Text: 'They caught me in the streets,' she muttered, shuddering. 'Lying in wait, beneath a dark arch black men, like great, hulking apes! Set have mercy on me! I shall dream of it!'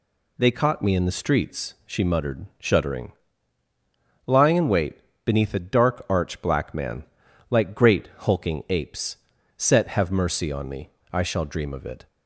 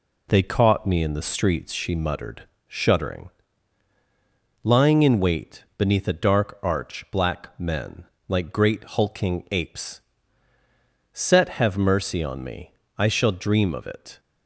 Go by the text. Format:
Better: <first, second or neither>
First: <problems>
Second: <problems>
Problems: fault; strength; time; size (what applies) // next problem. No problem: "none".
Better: second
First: says "man" for "men"; at 6.7 s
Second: none